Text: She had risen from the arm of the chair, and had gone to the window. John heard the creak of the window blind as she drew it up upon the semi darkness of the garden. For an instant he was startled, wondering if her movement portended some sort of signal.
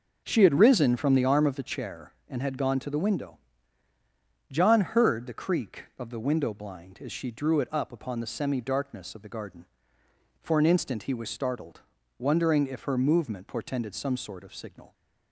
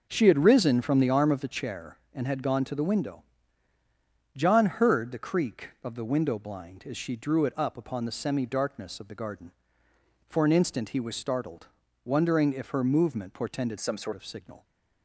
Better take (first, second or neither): first